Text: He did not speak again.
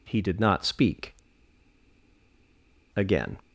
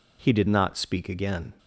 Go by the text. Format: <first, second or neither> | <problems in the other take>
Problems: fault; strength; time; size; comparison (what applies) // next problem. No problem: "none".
second | pauses between "speak" and "again"; strong; at 1.1 s; 1.8 s long